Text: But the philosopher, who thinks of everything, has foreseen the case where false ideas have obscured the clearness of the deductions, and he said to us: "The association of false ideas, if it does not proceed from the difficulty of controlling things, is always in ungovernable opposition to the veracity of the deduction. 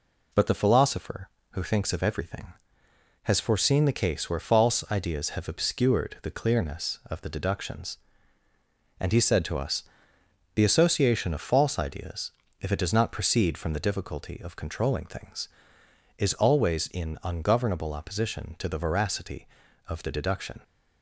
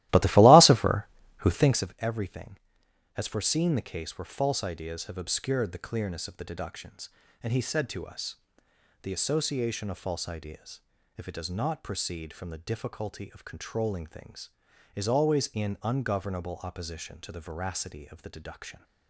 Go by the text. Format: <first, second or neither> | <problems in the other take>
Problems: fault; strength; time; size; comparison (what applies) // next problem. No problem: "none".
first | starts louder than the rest; strong; until 1.9 s; 16 dB